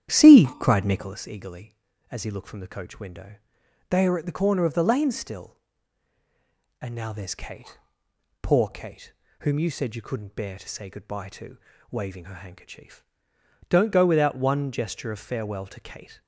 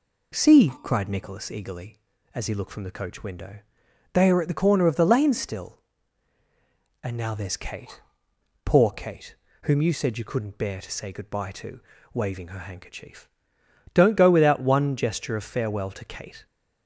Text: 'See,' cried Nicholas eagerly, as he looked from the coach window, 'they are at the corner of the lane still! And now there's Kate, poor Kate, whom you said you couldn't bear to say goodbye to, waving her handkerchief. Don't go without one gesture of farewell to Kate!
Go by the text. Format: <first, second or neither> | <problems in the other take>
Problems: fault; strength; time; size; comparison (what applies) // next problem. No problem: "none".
second | starts louder than the rest; strong; until 1.2 s; 10.5 dB